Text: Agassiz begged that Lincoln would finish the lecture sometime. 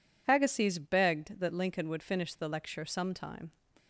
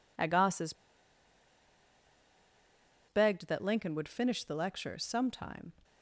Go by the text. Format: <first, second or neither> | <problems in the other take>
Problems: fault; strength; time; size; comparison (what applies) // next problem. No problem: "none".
first | pauses between "Agassiz" and "begged"; strong; at 0.7 s; 2.3 s long